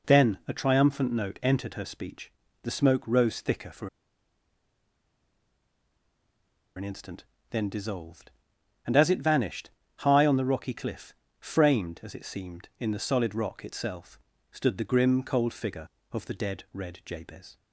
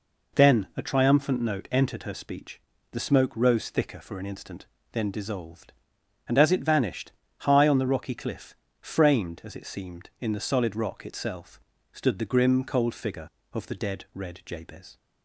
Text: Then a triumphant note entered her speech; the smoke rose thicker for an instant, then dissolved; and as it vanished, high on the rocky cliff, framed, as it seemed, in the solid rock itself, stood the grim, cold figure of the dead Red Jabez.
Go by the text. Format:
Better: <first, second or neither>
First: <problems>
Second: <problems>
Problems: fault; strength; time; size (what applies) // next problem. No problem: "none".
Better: second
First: pauses between "for" and "an"; strong; at 3.8 s; 2.8 s long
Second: none